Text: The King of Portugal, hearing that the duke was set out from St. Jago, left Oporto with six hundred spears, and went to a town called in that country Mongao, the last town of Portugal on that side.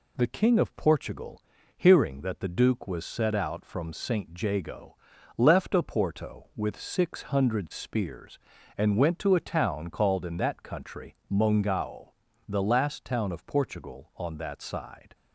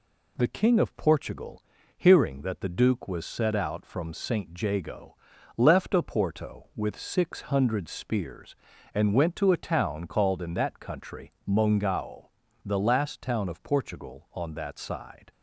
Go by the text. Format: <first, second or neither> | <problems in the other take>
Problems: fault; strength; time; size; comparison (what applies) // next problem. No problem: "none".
neither | pauses between "country" and "Mongao"; slight; the same in both